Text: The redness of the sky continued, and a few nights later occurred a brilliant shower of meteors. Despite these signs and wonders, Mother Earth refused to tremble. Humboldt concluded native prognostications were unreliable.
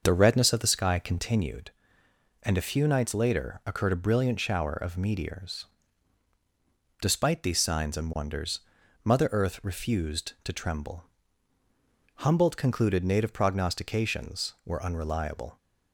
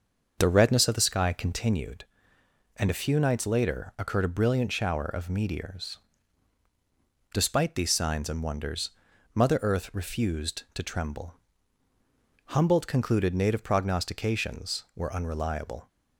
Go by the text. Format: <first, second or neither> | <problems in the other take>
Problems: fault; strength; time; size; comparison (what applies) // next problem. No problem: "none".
neither | starts louder than the rest; the same in both